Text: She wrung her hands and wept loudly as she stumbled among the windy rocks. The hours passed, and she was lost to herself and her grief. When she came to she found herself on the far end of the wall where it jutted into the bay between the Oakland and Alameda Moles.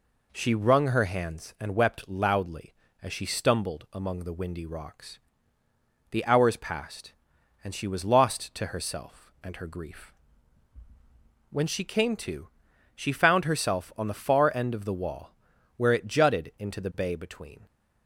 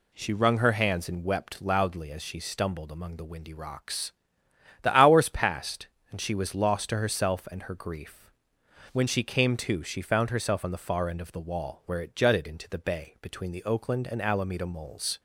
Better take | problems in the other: second | pauses between "to" and "she"; noticeable; at 12.4 s; 0.46 s long // pauses between "wall" and "where"; at 15.3 s; 0.44 s long // stops before "the Oakland and Alameda Moles"; at 17.6 s

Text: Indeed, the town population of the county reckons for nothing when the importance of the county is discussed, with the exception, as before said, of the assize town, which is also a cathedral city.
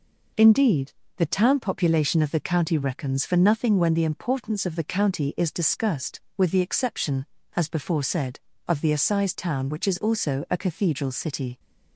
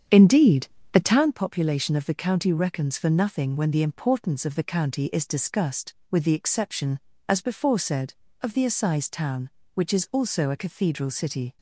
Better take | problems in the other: first | starts louder than the rest; strong; until 1.3 s; 8 dB

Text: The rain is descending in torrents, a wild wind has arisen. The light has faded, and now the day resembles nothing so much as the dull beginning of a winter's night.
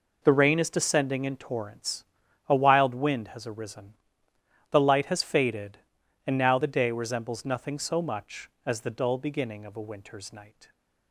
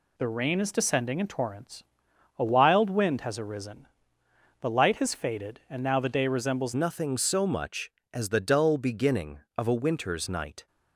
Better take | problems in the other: first | changes voice at "nothing"; from 6.7 s on; 3.9 s long

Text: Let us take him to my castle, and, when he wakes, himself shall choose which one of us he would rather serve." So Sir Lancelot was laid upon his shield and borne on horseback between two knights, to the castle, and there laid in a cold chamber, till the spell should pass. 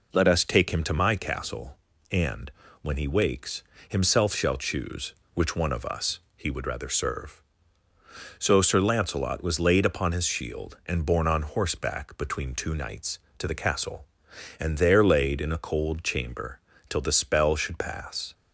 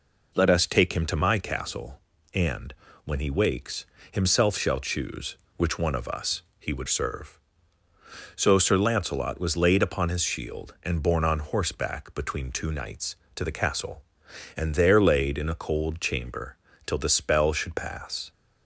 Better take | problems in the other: first | pauses between "us" and "he"; slight; at 6.4 s; 0.18 s long; slight in the first // skips "rather"; at 6.8 s

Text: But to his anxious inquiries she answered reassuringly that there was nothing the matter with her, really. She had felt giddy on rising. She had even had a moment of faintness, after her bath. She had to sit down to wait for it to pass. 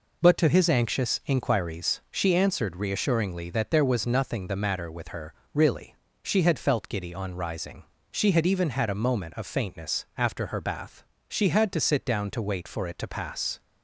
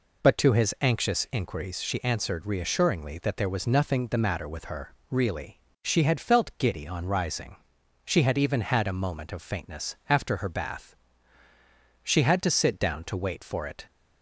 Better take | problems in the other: first | stops before "to pass"; at 13.8 s

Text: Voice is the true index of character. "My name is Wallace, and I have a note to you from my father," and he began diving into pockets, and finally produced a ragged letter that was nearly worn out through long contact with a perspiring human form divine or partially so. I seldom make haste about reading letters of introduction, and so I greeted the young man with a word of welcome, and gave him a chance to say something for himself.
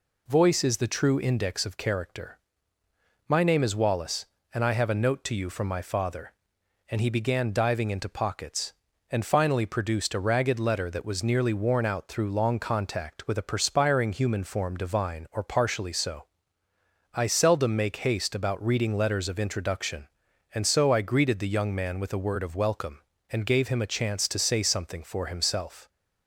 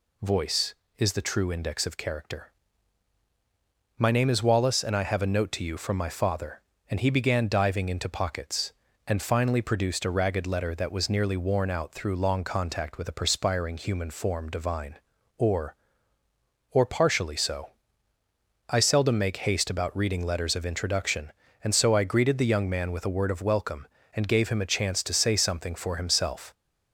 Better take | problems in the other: first | says "or" twice; at 16.7 s

